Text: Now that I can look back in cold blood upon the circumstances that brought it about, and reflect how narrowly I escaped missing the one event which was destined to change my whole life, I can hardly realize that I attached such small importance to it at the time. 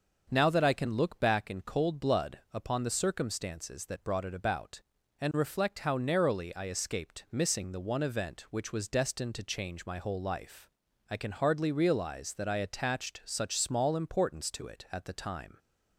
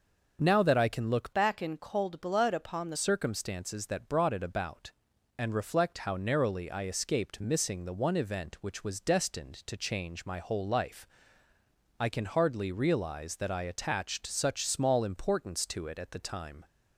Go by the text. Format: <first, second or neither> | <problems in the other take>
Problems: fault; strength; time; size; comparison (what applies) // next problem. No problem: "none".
first | starts louder than the rest; until 1.4 s; 6 dB; also in the first // changes voice from "back" to "the"; from 1.3 to 2.9 s; 1.6 s long